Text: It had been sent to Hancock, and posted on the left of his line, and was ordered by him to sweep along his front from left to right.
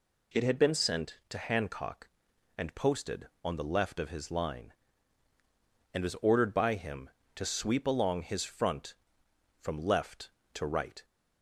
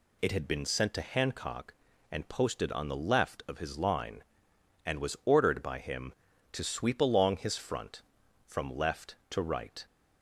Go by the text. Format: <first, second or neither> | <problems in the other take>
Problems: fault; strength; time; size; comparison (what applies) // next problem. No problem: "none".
neither | none